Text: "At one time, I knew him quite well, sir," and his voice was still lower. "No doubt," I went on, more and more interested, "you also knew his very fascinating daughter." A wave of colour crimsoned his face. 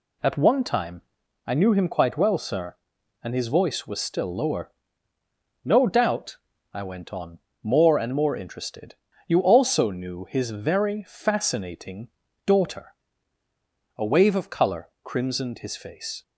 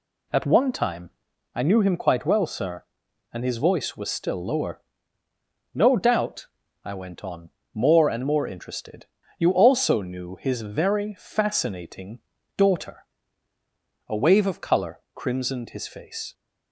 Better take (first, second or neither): neither